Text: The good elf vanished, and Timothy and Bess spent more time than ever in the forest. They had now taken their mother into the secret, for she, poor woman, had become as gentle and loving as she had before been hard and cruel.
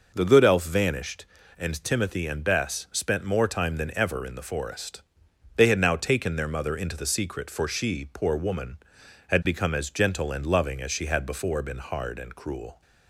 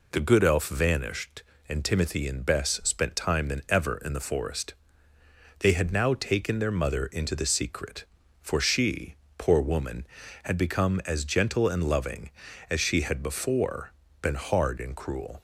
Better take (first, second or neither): first